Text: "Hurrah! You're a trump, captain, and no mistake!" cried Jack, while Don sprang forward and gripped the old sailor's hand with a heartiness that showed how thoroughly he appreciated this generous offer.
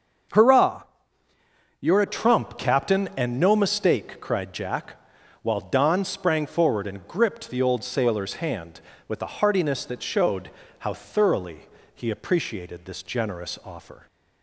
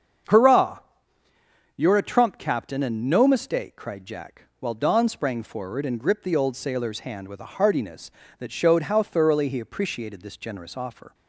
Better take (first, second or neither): second